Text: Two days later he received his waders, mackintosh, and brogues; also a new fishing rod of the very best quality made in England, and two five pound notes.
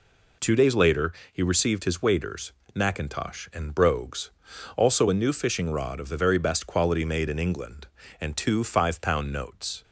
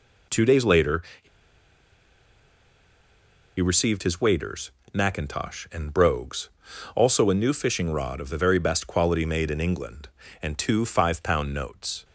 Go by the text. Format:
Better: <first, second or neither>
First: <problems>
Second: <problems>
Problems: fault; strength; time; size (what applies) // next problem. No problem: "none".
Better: first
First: pauses between "later" and "he"; slight; at 1.1 s; 0.20 s long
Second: pauses between "later" and "he"; slight; at 1.0 s; 0.20 s long // pauses between "he" and "received"; strong; at 1.2 s; 2.3 s long